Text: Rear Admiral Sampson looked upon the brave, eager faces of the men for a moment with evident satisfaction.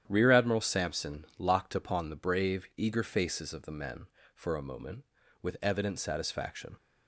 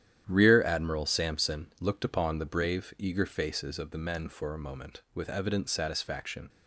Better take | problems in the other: second | starts louder than the rest; strong; until 1.0 s; 10 dB; strong in the second // says "locked" for "looked"; at 1.3 s

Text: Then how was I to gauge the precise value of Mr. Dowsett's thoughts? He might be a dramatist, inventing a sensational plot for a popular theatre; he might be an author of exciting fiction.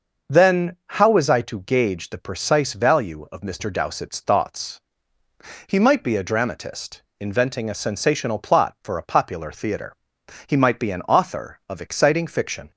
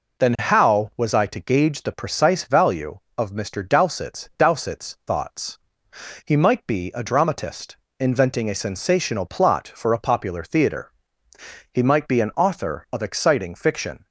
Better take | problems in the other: first | says "Dowsett's" twice; at 4.3 s

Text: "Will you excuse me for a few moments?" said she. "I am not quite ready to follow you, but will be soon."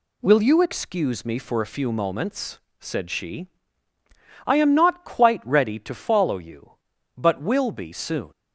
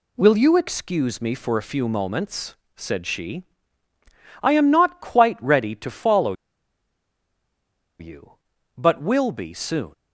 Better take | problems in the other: first | pauses between "follow" and "you"; strong; at 6.3 s; 1.6 s long

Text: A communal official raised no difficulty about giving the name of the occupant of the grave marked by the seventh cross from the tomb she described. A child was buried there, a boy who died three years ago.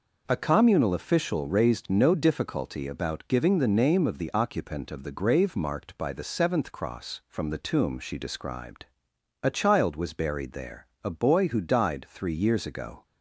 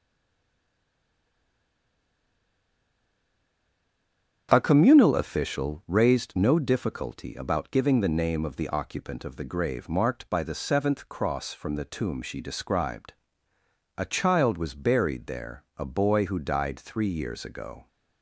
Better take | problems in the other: first | stays silent before the first word; strong; until 4.4 s; 4.4 s long // starts louder than the rest; strong; until 5.5 s; 8.5 dB

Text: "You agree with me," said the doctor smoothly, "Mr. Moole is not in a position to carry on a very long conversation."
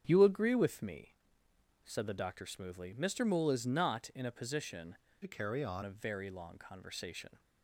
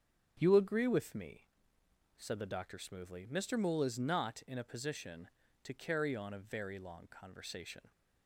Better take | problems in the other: second | starts louder than the rest; strong; until 1.0 s; 8 dB; strong in the second // changes voice from "to" to "on"; from 5.2 to 5.8 s; 0.6 s long

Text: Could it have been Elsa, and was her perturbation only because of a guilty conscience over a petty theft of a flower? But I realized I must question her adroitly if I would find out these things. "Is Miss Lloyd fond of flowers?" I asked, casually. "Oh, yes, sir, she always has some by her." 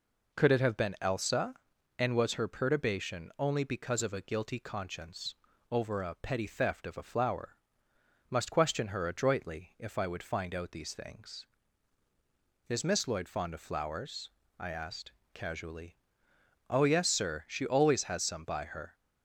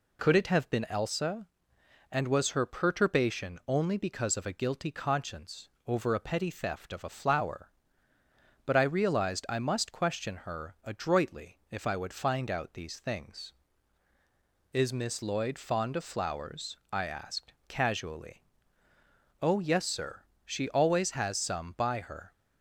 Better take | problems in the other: second | pauses between "conscience" and "over"; slight; at 5.3 s; 0.36 s long; slight in the second // skips "But I realized I"; at 7.9 s

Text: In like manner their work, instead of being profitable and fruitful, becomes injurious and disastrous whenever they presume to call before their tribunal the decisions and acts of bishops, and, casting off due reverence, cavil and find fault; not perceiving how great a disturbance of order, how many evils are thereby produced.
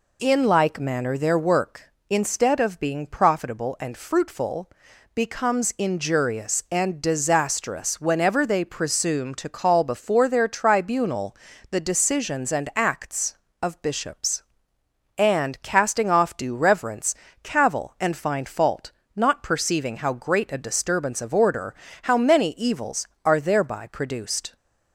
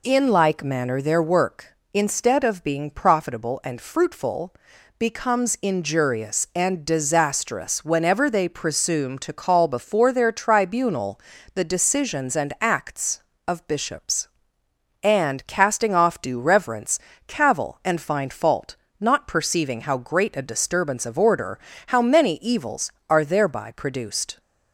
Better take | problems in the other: neither | pauses between "tribunal" and "the"; slight; the same in both

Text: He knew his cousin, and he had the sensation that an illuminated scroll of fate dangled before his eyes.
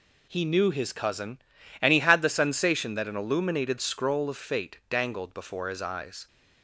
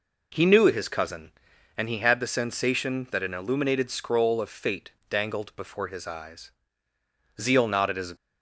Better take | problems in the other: first | pauses between "fate" and "dangled"; slight; at 4.8 s; 0.20 s long // goes on to say "Zeal nodded His"; noticeable; from 7.3 s on; 0.76 s long

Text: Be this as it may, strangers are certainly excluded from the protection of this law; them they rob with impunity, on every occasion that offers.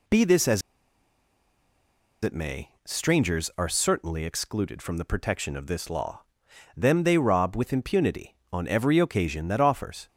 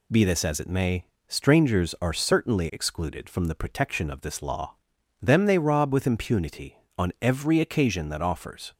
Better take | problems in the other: second | pauses between "as" and "it"; strong; at 0.6 s; 1.6 s long

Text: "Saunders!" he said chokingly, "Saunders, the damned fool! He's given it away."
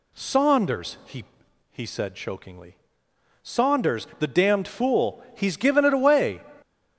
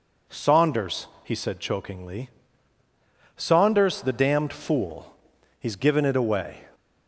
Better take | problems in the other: second | says "he" twice; at 1.7 s

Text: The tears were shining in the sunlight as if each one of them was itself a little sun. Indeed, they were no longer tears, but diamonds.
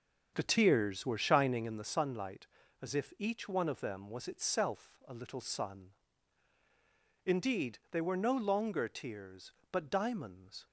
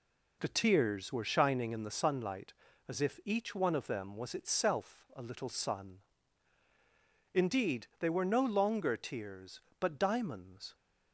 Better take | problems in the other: second | starts louder than the rest; until 1.8 s; 7 dB

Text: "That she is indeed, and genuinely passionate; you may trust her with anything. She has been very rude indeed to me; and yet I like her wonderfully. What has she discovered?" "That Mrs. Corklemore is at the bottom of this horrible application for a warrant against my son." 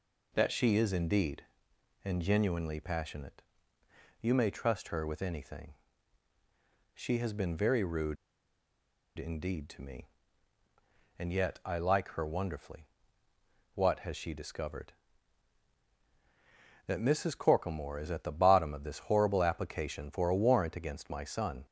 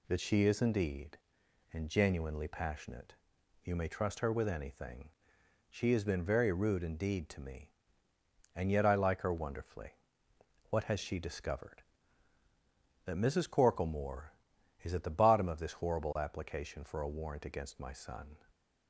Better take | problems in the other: second | pauses between "rude" and "indeed"; at 8.1 s; 1.0 s long

